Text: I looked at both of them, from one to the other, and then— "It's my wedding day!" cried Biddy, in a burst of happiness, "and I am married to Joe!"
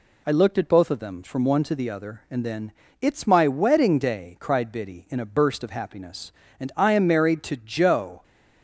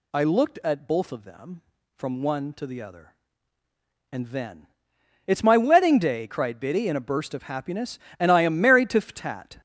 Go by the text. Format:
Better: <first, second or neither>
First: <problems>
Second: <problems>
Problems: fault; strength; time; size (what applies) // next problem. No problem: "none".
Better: first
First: none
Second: says "Ftat" for "Joe"; at 9.0 s